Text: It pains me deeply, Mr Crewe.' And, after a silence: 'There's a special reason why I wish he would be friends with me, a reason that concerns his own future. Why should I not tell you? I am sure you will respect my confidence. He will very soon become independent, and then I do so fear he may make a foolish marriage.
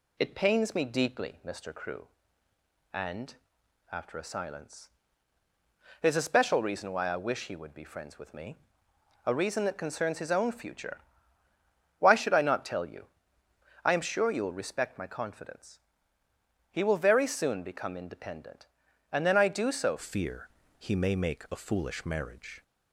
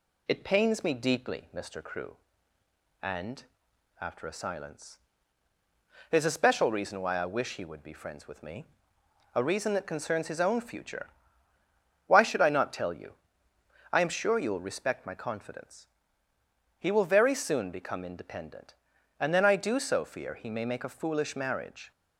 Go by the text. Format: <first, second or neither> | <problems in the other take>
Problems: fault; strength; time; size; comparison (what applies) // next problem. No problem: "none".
second | changes voice at "fear"; from 19.9 s on; 2.7 s long // pauses between "fear" and "he"; slight; at 20.4 s; 0.30 s long